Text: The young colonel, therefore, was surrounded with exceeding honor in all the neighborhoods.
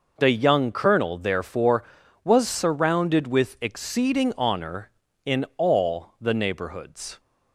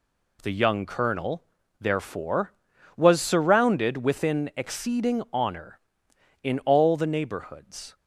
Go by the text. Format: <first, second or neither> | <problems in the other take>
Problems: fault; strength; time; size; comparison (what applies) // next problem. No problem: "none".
first | says "within" for "with"; at 3.9 s